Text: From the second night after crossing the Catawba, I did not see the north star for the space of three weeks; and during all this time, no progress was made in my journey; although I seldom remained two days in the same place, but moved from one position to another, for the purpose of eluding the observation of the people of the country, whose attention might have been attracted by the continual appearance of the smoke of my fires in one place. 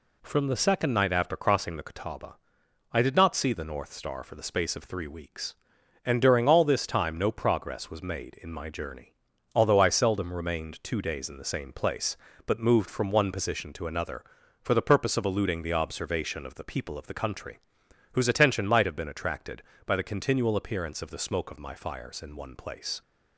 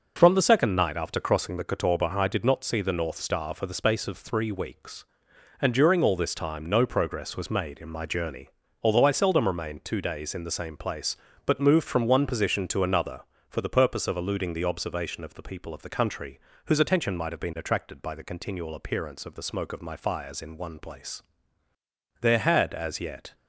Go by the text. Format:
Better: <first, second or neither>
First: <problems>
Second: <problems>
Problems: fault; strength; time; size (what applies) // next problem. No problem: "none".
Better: first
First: none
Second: goes on to say "There had as yet"; noticeable; from 22.1 s on; 1.1 s long